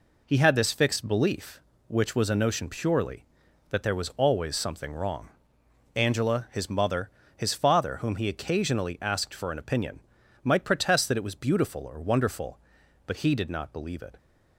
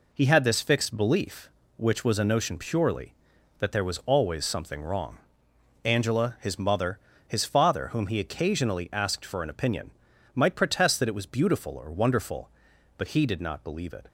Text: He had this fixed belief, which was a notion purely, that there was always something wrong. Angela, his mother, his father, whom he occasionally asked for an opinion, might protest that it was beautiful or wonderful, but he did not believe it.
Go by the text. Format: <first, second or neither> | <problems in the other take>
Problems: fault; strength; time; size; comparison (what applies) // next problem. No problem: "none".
neither | none